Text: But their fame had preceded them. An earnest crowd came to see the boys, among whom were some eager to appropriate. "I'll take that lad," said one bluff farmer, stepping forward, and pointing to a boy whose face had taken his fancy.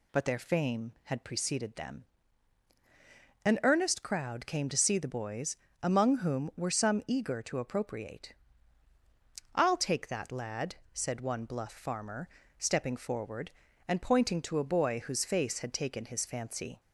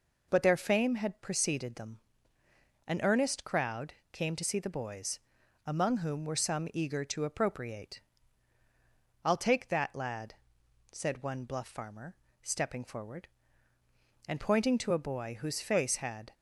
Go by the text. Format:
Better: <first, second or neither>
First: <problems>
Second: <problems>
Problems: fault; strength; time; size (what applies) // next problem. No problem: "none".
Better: first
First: none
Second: pauses between "crowd" and "came"; slight; at 3.9 s; 0.18 s long // stops before "taken his fancy"; at 16.3 s